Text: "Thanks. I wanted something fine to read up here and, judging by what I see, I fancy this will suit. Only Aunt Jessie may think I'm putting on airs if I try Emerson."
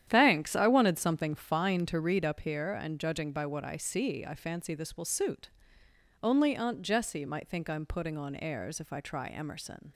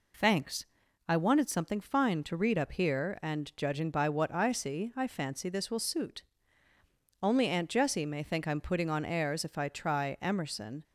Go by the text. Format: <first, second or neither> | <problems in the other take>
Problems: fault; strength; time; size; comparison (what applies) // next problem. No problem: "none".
second | starts louder than the rest; strong; until 1.1 s; 10 dB // says "might" for "may"; at 7.2 s